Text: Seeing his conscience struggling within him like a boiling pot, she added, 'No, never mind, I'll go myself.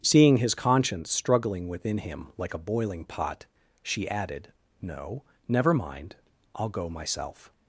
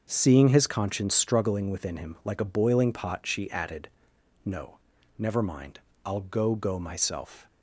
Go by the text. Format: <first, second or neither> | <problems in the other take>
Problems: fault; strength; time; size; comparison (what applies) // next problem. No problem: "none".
first | starts louder than the rest; until 1.1 s; 6.5 dB; strong in the first // says "go" twice; at 6.5 s